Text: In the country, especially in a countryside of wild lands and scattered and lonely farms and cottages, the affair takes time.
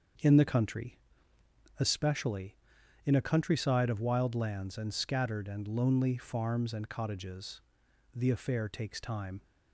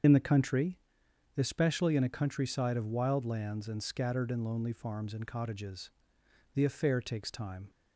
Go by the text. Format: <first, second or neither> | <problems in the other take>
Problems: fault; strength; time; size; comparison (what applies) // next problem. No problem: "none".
first | loses the start of "In"; at 0.0 s; 45 ms // starts louder than the rest; until 1.6 s; 7 dB; also in the first